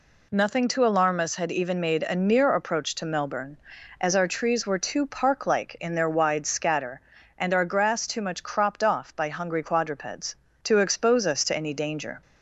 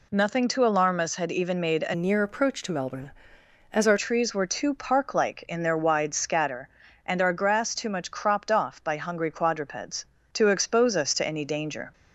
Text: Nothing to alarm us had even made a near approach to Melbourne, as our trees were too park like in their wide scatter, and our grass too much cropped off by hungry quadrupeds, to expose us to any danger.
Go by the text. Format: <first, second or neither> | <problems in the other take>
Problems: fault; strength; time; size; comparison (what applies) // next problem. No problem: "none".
first | changes voice from "near" to "our"; from 1.9 to 3.9 s; 2.0 s long